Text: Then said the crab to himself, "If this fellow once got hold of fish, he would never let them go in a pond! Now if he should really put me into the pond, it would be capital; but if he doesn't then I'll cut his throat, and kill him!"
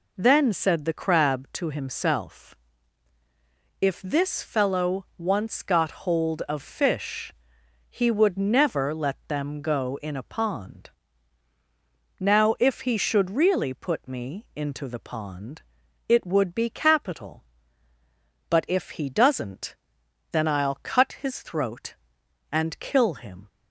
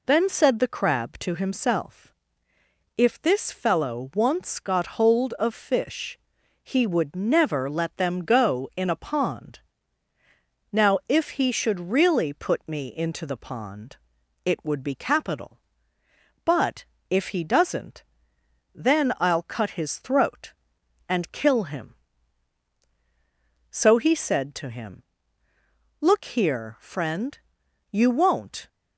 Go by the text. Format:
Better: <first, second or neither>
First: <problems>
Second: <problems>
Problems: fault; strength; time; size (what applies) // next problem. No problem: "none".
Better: first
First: pauses between "doesn't" and "then"; noticeable; at 19.7 s; 0.56 s long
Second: pauses between "but" and "if"; slight; at 16.8 s; 0.26 s long // pauses between "doesn't" and "then"; noticeable; at 18.0 s; 0.72 s long // goes on to say "So he said to him Look here friend you won't"; strong; from 23.7 s on; 4.9 s long